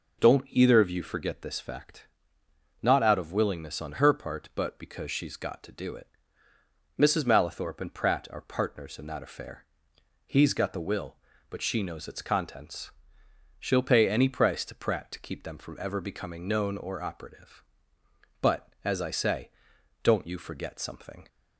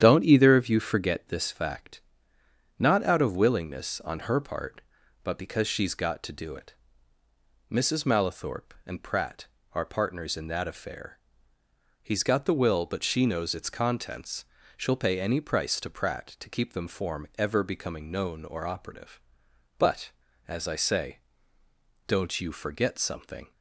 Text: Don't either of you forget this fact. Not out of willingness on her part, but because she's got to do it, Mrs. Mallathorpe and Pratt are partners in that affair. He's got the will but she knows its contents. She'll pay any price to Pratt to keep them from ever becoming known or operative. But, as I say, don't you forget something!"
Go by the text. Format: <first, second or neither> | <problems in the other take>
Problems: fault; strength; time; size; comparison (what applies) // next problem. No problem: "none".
first | starts louder than the rest; strong; until 1.0 s; 9.5 dB // says "form" for "from"; at 16.8 s